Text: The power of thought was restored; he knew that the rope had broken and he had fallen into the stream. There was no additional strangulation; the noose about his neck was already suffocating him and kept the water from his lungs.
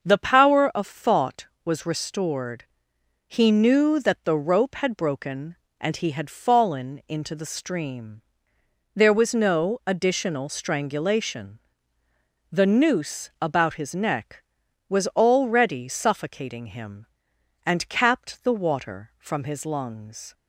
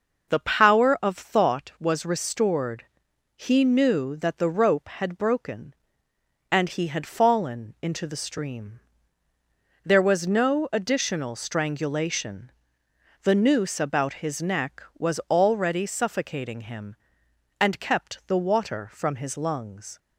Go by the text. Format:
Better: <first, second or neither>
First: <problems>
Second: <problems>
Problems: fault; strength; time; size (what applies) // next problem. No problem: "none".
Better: second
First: starts louder than the rest; until 1.1 s; 6.5 dB // says "capped" for "kept"; at 17.8 s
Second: none